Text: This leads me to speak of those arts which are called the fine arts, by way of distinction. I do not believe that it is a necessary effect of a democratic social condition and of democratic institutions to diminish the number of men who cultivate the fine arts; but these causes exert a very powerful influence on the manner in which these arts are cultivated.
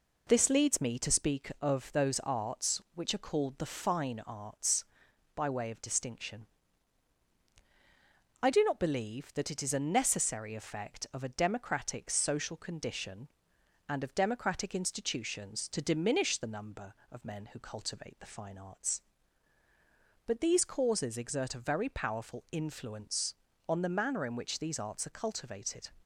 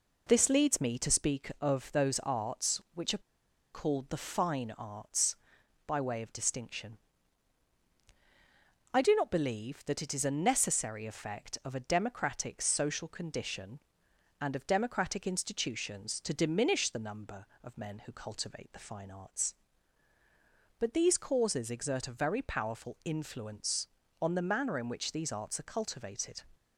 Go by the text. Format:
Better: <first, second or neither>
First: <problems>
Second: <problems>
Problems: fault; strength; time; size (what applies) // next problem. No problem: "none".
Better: first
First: none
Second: pauses between "are" and "called"; noticeable; at 3.2 s; 0.53 s long